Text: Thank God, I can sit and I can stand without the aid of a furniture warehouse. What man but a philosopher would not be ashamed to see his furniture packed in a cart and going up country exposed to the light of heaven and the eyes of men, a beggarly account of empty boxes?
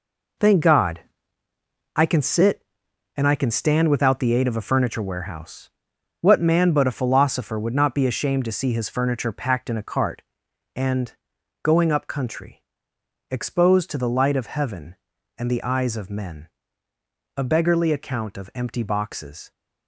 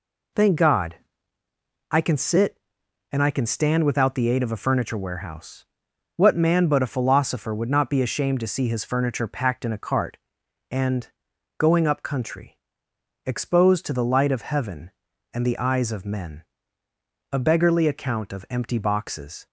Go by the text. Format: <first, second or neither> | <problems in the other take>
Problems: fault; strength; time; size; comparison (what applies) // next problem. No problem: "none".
second | gets quieter; strong; throughout; 9 dB // pauses between "and" and "going"; noticeable; at 11.1 s; 0.52 s long; noticeable in the second // pauses between "country" and "exposed"; noticeable; at 12.6 s; 0.70 s long; noticeable in the second